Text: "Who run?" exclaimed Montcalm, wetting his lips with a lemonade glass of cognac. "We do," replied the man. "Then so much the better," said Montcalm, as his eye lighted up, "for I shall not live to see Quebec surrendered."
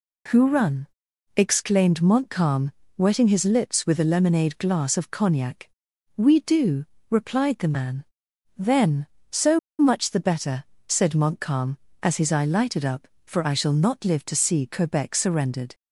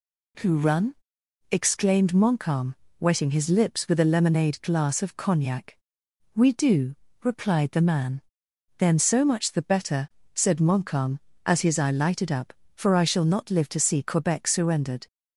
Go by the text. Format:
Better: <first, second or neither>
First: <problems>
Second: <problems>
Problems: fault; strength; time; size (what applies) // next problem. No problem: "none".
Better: second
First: pauses between "so" and "much"; slight; at 9.5 s; 0.21 s long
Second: none